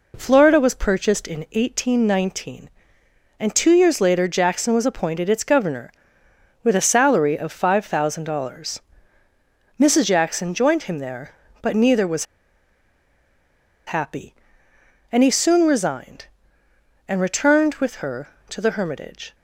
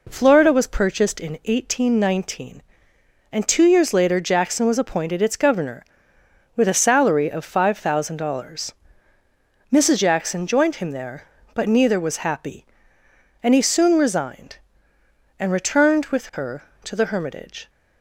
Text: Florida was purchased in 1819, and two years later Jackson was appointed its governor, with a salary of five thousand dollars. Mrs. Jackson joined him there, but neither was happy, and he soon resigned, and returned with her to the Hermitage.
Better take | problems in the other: second | pauses between "was" and "happy"; strong; at 12.2 s; 1.6 s long

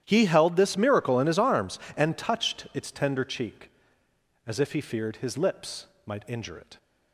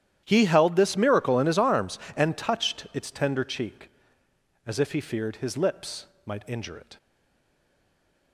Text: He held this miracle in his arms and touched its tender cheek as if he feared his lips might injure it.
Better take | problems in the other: first | starts louder than the rest; strong; until 1.2 s; 11 dB; strong in the first // pauses between "lips" and "might"; slight; at 6.0 s; 0.20 s long; slight in the first // stays silent after the last word; noticeable; from 6.9 s on; 1.4 s long

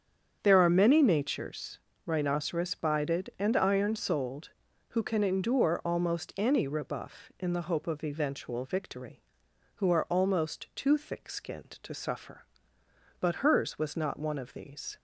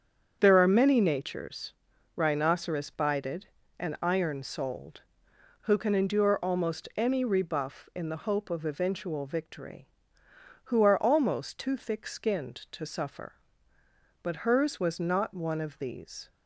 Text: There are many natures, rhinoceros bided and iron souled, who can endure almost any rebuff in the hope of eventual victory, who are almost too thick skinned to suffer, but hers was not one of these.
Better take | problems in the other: neither | starts louder than the rest; strong; the same in both

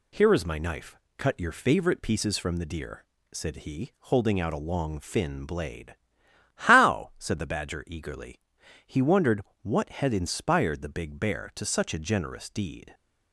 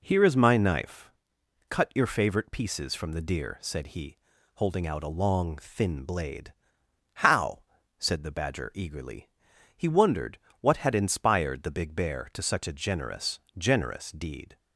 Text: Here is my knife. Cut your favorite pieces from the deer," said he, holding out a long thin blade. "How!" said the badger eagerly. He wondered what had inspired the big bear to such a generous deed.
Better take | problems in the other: first | pauses between "wondered" and "what"; slight; at 10.3 s; 0.20 s long; slight in the first // says "generous" twice; at 13.5 s

